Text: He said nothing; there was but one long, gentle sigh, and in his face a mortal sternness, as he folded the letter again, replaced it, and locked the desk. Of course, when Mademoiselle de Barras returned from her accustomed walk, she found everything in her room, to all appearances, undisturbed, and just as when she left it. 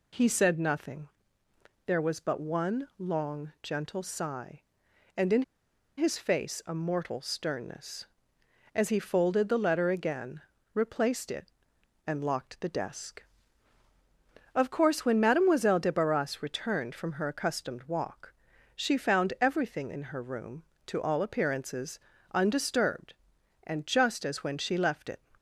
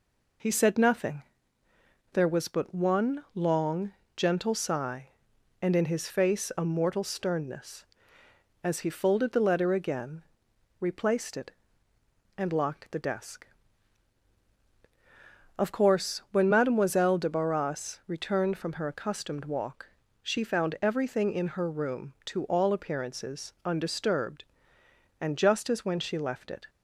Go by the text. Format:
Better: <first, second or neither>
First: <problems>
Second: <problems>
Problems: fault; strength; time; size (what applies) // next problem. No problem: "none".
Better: second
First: pauses between "in" and "his"; noticeable; at 5.4 s; 0.55 s long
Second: none